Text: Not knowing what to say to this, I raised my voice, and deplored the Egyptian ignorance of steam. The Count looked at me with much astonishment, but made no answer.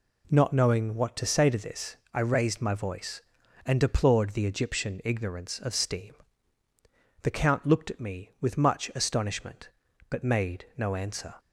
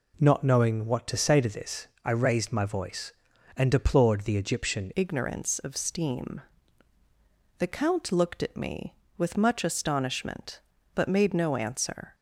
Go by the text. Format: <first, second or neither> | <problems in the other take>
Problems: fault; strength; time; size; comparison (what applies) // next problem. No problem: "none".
first | changes voice at "ignorance"; from 4.9 s on; 7.2 s long